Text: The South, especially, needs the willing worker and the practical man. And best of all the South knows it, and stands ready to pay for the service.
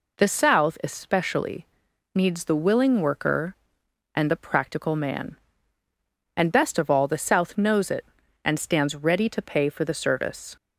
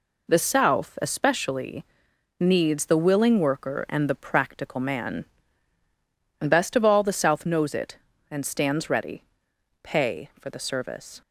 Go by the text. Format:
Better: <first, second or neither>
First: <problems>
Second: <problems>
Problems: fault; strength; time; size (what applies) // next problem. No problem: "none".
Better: first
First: none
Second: skips "to"; at 9.5 s